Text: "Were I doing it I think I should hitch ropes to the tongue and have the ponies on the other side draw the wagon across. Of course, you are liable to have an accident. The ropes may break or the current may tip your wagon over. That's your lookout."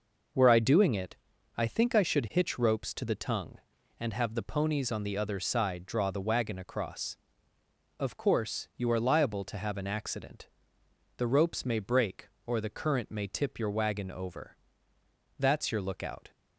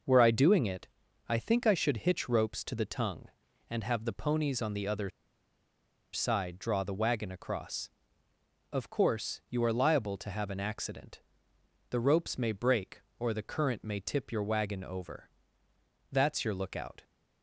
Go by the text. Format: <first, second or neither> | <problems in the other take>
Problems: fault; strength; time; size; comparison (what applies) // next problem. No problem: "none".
first | pauses between "it" and "I"; at 0.8 s; 0.40 s long; also in the first // pauses between "other" and "side"; at 5.0 s; 1.0 s long